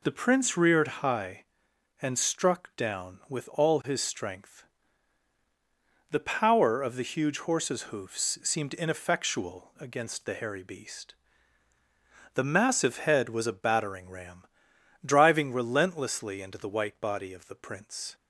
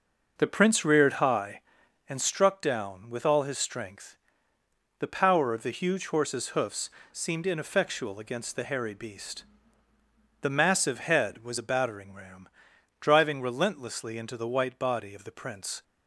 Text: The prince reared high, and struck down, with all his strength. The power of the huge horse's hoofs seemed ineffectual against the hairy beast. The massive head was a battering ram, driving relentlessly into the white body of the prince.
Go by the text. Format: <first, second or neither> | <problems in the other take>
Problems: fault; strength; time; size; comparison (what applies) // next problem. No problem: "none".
first | starts louder than the rest; noticeable; until 2.3 s; 6 dB // pauses between "hoofs" and "seemed"; slight; at 6.8 s; 0.20 s long